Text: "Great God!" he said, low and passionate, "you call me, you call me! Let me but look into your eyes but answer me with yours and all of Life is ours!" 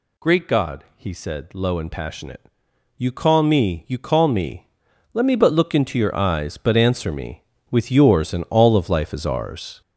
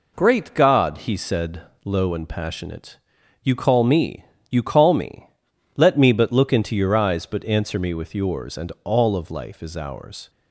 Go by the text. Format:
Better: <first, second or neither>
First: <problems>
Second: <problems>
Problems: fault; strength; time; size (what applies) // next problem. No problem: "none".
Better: second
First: gets louder; strong; throughout; 8 dB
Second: none